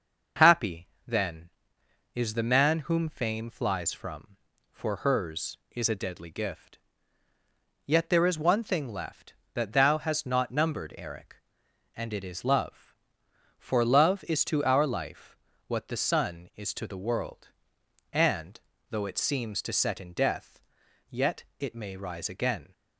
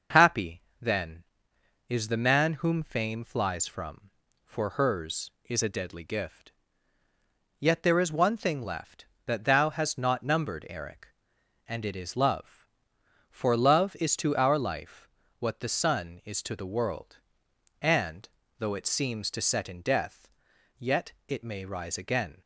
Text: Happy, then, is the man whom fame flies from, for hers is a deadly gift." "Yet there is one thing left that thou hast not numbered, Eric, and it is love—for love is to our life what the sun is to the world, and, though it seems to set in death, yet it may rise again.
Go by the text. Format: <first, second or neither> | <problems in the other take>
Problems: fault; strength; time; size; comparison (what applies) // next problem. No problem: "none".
neither | pauses between "life" and "what"; slight; the same in both